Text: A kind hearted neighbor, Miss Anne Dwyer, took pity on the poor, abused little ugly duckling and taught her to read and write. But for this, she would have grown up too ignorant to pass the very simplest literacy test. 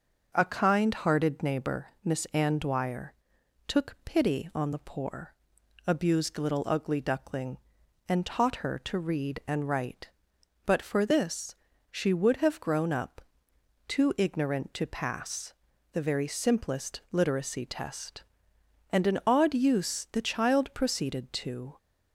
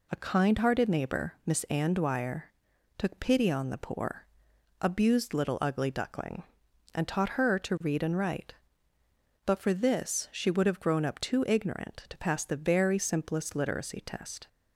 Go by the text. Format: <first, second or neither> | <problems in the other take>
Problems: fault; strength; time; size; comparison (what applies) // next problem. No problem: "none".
second | starts louder than the rest; noticeable; until 1.3 s; 6 dB // pauses between "up" and "too"; noticeable; at 13.1 s; 0.70 s long // pauses between "pass" and "the"; at 15.5 s; 0.40 s long // goes on to say "And an odd use the child proceeded to"; strong; from 18.8 s on; 2.8 s long